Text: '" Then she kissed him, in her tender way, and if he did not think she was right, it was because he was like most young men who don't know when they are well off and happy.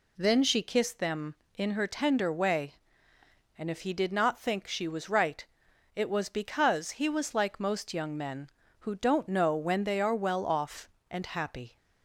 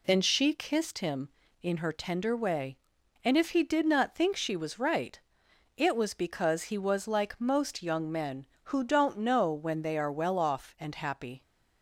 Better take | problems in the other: second | says "them" for "him"; at 0.9 s

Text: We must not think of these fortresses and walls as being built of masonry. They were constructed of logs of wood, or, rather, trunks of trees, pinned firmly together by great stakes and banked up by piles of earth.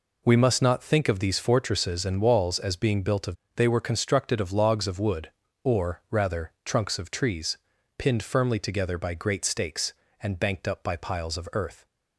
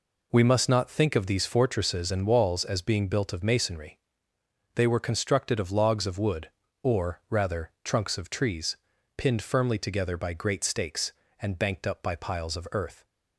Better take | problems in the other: second | skips "masonry"; at 3.4 s

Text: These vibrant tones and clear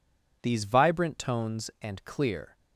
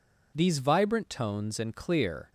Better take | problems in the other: neither | none

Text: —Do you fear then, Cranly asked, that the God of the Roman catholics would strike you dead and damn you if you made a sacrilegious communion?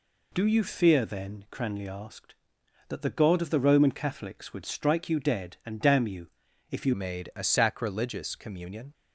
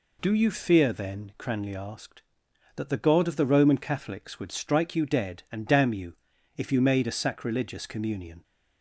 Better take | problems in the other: second | pauses between "you" and "if"; at 6.2 s; 0.44 s long; also in the second // changes voice at "made"; from 6.9 s on; 2.0 s long

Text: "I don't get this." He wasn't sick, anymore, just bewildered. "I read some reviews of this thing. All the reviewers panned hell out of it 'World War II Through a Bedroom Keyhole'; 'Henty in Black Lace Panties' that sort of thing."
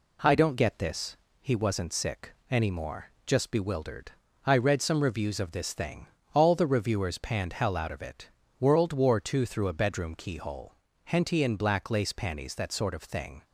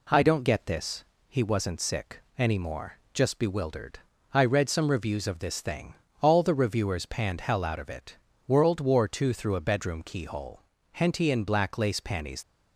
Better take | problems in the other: first | pauses between "it" and "World"; slight; at 8.1 s; 0.32 s long; slight in the first // stops before "that sort of thing"; at 12.4 s

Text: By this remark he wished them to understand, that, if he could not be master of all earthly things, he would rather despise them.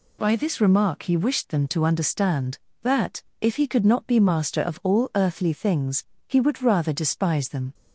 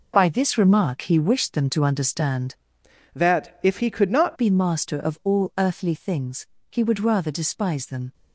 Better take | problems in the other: first | changes voice from "that" to "not"; from 3.1 to 4.3 s; 1.2 s long

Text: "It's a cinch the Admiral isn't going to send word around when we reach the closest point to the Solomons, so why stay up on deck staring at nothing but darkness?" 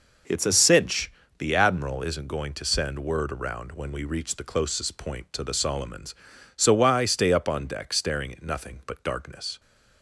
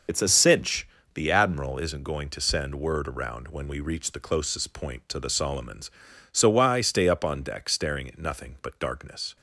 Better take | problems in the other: first | loses the start of "It's"; at 0.0 s; 70 ms // pauses between "cinch" and "the"; slight; at 0.8 s; 0.26 s long; slight in the first

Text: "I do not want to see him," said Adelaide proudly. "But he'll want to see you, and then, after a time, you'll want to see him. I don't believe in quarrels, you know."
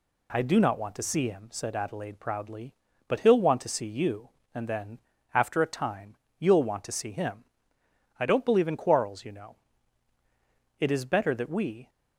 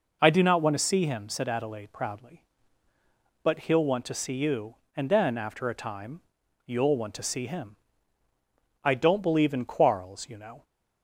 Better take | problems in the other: second | goes on to say "It is better that we"; noticeable; from 10.7 s on; 1.1 s long

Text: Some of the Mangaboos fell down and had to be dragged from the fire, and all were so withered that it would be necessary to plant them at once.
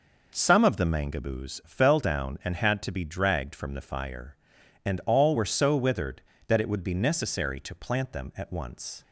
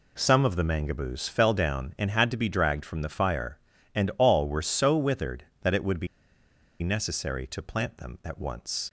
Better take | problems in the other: first | pauses between "be" and "necessary"; noticeable; at 6.0 s; 0.74 s long

